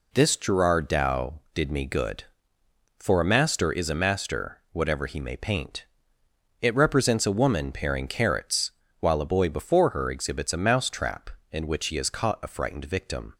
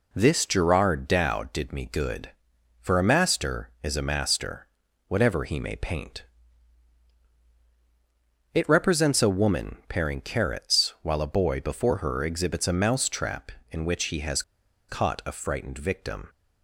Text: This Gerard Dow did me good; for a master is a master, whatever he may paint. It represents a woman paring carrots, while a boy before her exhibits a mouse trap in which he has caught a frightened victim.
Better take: first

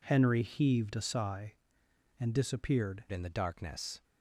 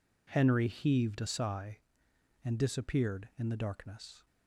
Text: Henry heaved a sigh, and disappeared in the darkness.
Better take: second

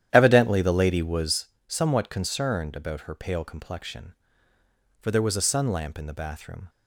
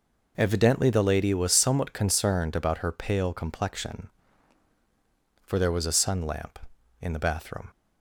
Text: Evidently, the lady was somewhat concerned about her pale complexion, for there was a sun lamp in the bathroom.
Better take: second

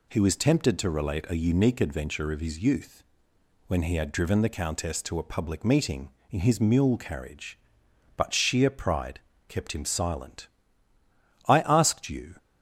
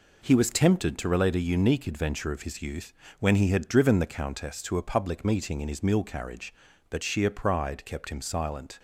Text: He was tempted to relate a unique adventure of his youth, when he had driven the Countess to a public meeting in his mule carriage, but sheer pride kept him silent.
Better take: second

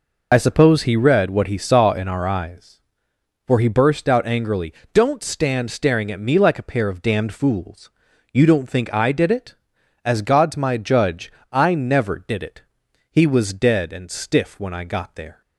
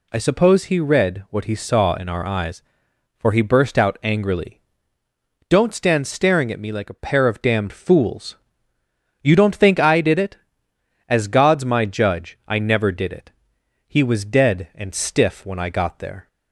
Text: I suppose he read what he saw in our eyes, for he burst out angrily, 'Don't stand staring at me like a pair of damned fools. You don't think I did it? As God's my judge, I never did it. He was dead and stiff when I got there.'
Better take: second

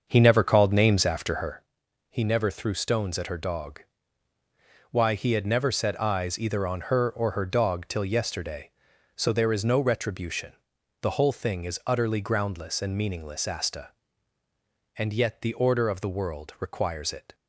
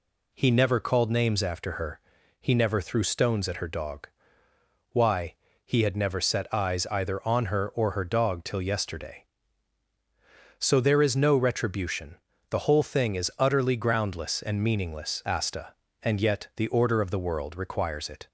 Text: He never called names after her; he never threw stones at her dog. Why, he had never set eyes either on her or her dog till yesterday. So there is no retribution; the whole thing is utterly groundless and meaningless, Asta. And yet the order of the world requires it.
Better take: second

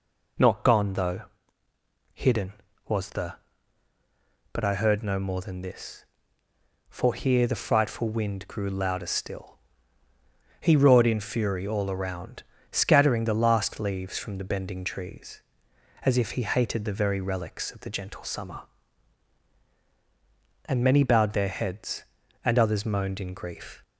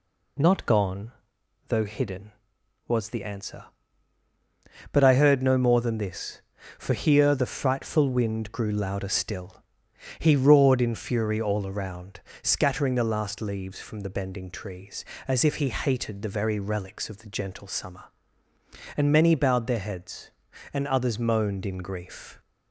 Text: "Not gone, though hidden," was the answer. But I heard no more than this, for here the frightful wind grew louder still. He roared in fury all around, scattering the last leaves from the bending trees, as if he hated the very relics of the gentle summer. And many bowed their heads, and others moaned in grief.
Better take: second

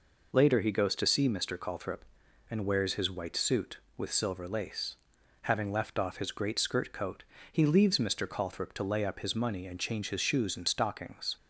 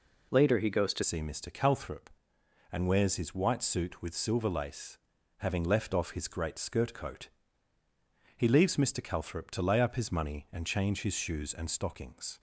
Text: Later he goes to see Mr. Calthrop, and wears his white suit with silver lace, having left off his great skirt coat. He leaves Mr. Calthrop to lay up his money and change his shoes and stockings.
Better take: first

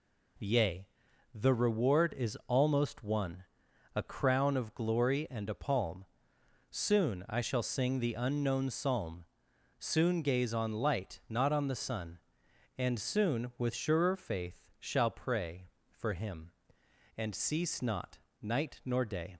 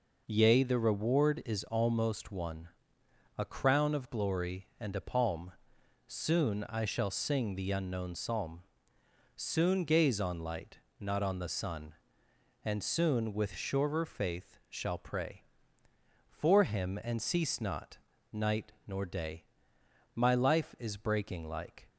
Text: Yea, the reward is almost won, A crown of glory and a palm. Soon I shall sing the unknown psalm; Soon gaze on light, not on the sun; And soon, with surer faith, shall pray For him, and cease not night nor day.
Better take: first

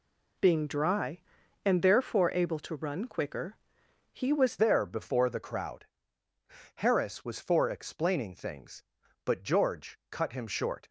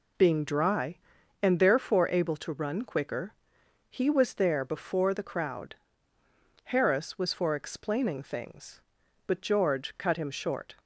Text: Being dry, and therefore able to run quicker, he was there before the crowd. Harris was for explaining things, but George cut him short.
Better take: second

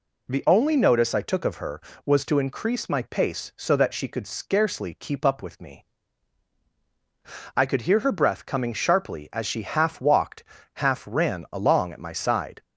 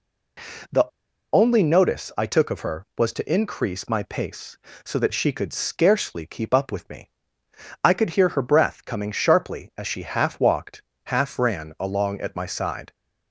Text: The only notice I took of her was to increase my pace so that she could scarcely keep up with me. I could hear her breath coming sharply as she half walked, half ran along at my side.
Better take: first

